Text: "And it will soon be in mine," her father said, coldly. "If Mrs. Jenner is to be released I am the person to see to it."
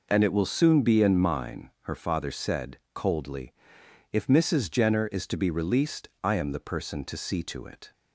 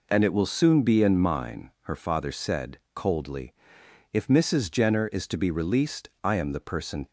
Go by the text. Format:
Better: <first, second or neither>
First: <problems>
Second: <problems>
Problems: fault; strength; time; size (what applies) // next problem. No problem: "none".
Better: first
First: pauses between "released" and "I"; slight; at 6.0 s; 0.16 s long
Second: pauses between "released" and "I"; slight; at 6.0 s; 0.16 s long // stops before "to see to it"; at 7.0 s